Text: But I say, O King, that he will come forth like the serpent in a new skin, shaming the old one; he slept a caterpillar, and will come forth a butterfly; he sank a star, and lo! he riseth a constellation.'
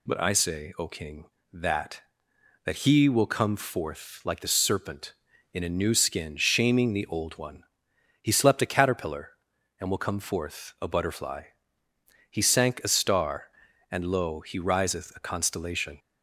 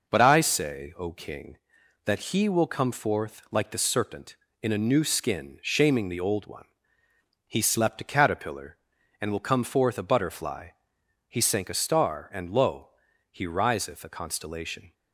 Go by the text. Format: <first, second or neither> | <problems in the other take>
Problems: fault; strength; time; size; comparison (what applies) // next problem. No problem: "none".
second | says "that" twice; at 2.6 s